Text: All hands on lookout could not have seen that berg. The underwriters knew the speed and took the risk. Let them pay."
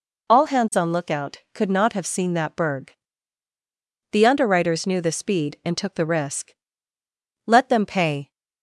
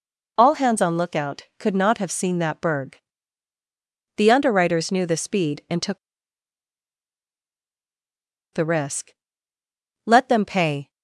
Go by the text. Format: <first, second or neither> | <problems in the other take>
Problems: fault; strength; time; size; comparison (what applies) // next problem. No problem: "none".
first | pauses between "took" and "the"; strong; at 5.9 s; 2.5 s long